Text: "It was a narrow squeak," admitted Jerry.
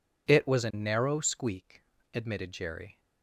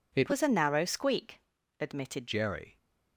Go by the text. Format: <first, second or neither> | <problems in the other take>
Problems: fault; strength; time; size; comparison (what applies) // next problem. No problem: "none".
first | changes voice from "was" to "admitted"; from 0.2 to 2.2 s; 2.0 s long